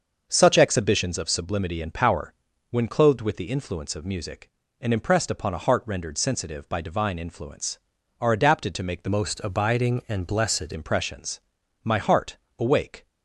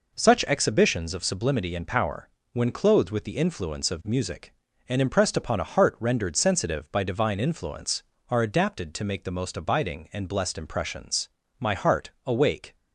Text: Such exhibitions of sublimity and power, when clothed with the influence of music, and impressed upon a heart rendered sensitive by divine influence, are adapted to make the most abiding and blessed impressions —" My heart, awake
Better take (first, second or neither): second